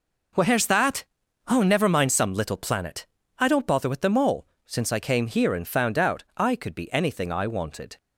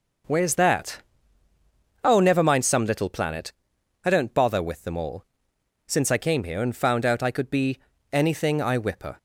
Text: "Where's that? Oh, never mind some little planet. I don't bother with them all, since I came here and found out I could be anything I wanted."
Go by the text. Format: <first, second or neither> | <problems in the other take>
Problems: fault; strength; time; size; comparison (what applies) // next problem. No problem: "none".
first | pauses between "be" and "anything"; slight; at 7.7 s; 0.34 s long // says "whipper" for "wanted"; at 8.7 s